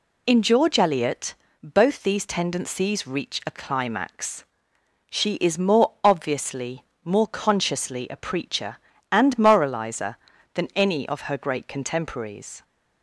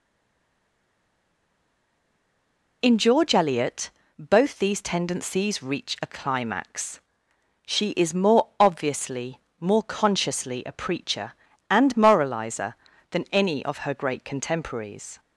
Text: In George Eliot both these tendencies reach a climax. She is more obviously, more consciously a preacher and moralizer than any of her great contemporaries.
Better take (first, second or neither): first